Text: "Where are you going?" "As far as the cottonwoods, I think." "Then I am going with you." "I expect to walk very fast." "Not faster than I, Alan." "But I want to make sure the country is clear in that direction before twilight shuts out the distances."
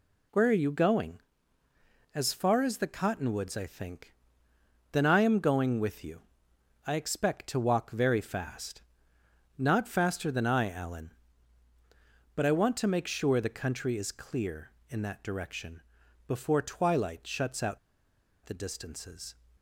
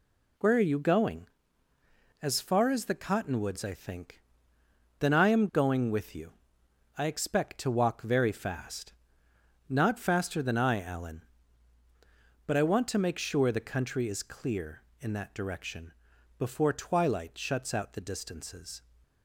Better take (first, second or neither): second